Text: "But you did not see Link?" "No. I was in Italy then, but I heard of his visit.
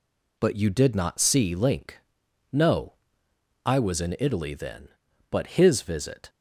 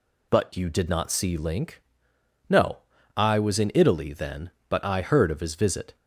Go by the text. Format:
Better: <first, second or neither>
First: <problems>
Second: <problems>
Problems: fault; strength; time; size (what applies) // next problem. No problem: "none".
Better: second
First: skips "I heard of"; at 5.4 s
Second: none